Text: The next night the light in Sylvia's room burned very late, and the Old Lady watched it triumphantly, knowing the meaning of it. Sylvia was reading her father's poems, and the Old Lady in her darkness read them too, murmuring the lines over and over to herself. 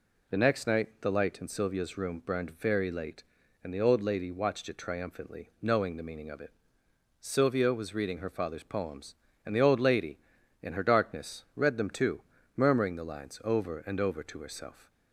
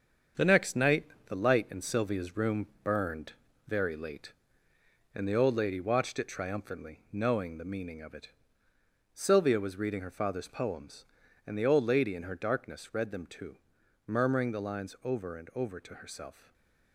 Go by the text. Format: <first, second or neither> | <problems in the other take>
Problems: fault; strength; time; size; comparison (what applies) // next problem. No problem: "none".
first | gets quieter; strong; throughout; 7.5 dB // pauses between "night" and "the"; slight; at 1.0 s; 0.22 s long // pauses between "room" and "burned"; slight; at 2.6 s; 0.16 s long // pauses between "burned" and "very"; slight; at 3.3 s; 0.36 s long // stays silent after the last word; slight; from 16.3 s on; 0.6 s long